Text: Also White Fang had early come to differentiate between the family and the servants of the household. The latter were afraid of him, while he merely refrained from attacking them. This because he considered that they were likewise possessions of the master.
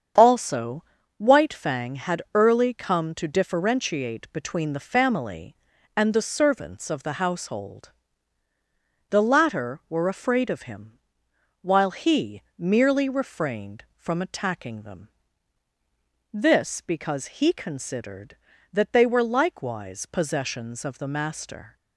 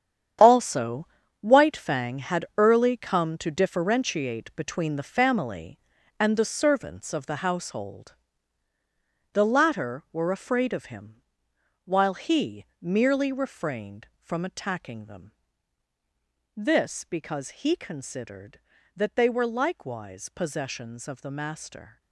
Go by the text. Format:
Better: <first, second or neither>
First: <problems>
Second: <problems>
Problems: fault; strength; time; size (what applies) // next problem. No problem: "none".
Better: first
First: starts louder than the rest; strong; until 1.5 s; 7.5 dB // pauses between "Also" and "White"; slight; at 0.8 s; 0.36 s long // pauses between "he" and "merely"; slight; at 12.4 s; 0.18 s long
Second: gets quieter; strong; throughout; 11.5 dB // starts louder than the rest; strong; until 1.7 s; 9 dB // pauses between "Also" and "White"; slight; at 1.0 s; 0.36 s long // pauses between "he" and "merely"; slight; at 12.6 s; 0.18 s long